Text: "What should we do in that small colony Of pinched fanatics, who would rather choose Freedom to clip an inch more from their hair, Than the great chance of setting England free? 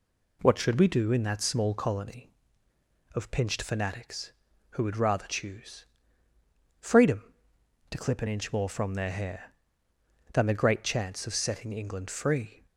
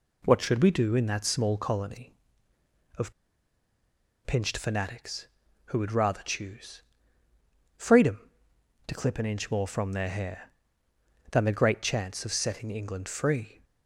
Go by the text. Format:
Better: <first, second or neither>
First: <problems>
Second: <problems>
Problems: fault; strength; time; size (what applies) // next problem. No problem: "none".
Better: first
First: pauses between "choose" and "Freedom"; noticeable; at 5.8 s; 0.94 s long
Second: pauses between "Of" and "pinched"; at 3.1 s; 1.1 s long // pauses between "choose" and "Freedom"; noticeable; at 6.8 s; 0.94 s long